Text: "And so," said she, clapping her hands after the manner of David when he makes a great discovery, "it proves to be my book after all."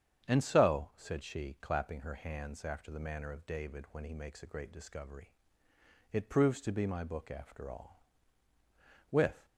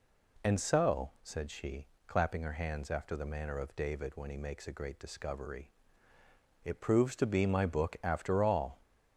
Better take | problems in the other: second | starts louder than the rest; strong; until 1.2 s; 8 dB // goes on to say "With"; slight; from 9.1 s on; 0.34 s long

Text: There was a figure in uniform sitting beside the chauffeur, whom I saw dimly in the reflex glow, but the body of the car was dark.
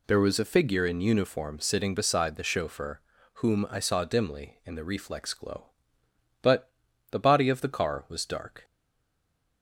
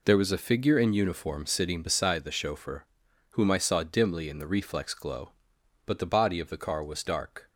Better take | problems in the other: second | pauses between "but" and "the"; at 6.7 s; 0.40 s long // stays silent after the last word; from 8.6 s on; 1.0 s long

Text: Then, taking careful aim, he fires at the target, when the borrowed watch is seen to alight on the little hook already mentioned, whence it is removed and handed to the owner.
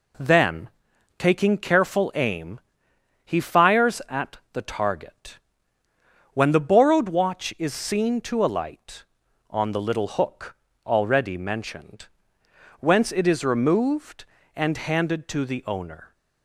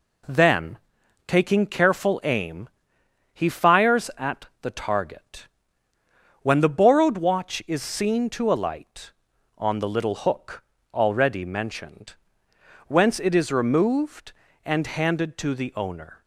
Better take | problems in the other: neither | pauses between "at" and "the"; slight; the same in both // pauses between "hook" and "already"; slight; the same in both

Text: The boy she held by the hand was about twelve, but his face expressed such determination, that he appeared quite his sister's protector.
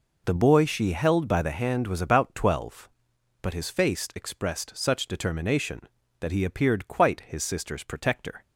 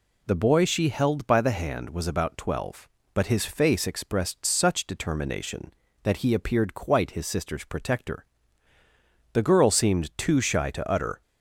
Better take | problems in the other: first | goes on to say "The girl seemed too shy to utter"; strong; from 9.3 s on; 1.8 s long

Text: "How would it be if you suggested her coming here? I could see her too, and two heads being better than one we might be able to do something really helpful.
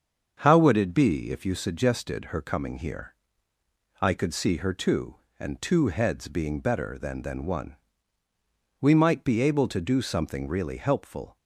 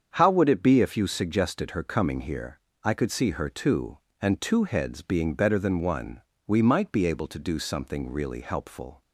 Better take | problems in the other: second | starts louder than the rest; until 1.4 s; 7 dB; strong in the second // says "than" twice; at 7.2 s // pauses between "one" and "we"; at 7.7 s; 1.0 s long; slight in the second

